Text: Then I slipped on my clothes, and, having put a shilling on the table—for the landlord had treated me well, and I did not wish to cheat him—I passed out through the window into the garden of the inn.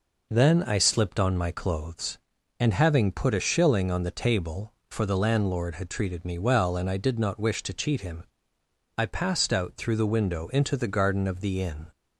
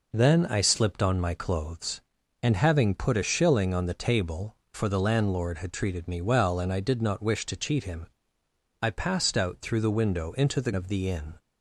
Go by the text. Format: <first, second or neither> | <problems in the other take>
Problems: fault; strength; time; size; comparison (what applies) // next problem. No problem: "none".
first | skips "garden"; at 10.7 s